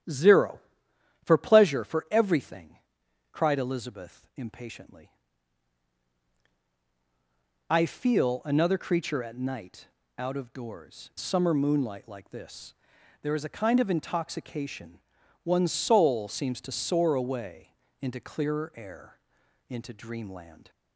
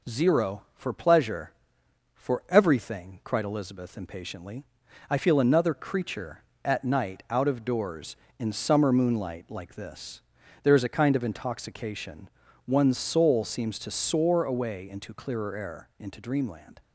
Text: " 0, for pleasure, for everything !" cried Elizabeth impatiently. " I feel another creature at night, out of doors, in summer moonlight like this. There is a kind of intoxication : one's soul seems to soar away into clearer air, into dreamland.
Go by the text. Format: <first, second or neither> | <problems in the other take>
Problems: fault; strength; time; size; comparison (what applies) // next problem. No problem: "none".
second | starts louder than the rest; strong; until 1.7 s; 12 dB // skips "in"; at 11.1 s // pauses between "away" and "into"; slight; at 17.7 s; 0.26 s long